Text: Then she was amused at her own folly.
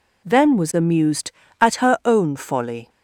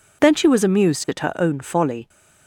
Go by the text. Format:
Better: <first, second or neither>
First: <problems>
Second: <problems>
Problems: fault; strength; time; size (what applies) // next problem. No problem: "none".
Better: second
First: skips "she"; at 0.5 s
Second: none